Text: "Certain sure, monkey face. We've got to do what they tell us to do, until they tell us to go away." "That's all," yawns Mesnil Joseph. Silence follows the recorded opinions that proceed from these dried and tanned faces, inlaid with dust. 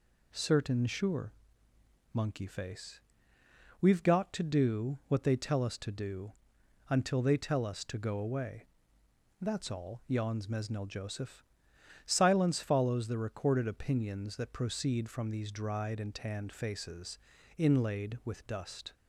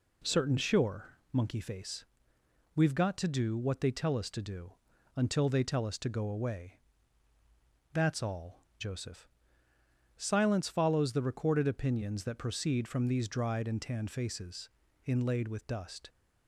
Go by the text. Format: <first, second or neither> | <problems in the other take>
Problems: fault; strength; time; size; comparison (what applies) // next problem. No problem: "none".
first | skips "yawns Mesnil"; at 8.7 s